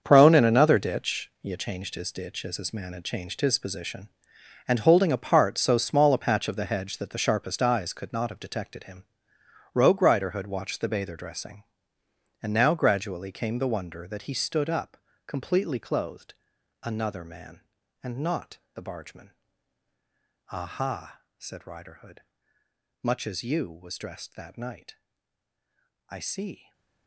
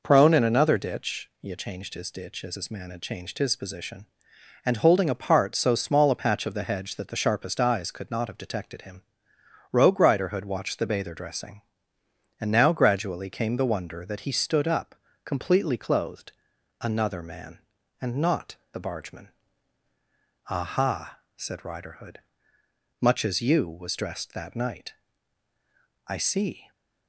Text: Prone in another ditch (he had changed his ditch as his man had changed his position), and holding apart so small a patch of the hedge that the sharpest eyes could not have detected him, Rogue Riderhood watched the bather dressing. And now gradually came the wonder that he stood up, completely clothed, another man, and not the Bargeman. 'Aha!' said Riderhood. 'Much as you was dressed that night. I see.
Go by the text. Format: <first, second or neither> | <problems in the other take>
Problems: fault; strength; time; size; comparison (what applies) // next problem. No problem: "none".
second | gets quieter; strong; throughout; 12 dB // pauses between "not" and "the"; slight; at 18.5 s; 0.16 s long; slight in the second // stays silent after the last word; slight; from 26.5 s on; 0.5 s long